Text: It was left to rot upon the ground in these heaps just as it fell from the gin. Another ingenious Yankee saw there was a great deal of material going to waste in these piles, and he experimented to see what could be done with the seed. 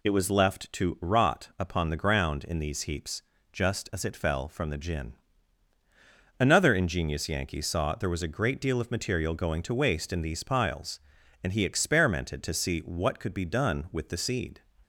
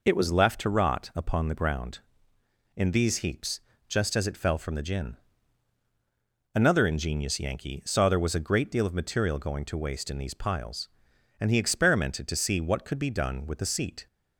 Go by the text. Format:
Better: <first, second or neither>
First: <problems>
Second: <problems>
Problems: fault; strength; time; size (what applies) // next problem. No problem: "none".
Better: first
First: pauses between "heaps" and "just"; slight; at 3.2 s; 0.30 s long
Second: pauses between "heaps" and "just"; slight; at 3.6 s; 0.26 s long // says "seat" for "seed"; at 13.6 s